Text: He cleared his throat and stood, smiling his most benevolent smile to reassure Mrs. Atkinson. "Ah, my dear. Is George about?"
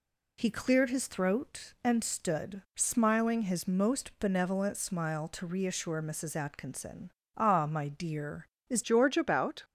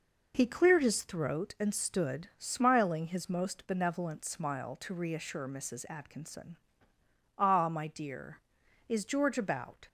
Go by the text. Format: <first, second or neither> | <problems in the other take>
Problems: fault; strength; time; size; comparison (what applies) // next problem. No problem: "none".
second | changes voice at "George"; from 8.8 s on; 0.8 s long